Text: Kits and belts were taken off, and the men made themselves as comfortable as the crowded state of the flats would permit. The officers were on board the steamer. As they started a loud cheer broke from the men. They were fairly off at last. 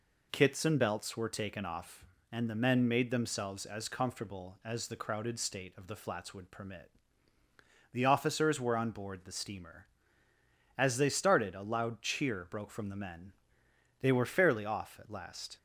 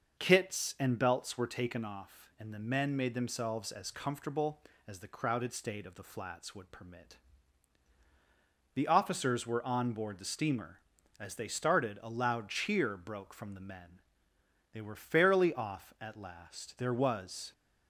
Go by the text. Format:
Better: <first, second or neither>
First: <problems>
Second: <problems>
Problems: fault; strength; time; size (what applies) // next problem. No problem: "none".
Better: first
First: none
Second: starts louder than the rest; noticeable; until 1.2 s; 6 dB // goes on to say "There was"; noticeable; from 16.7 s on; 0.76 s long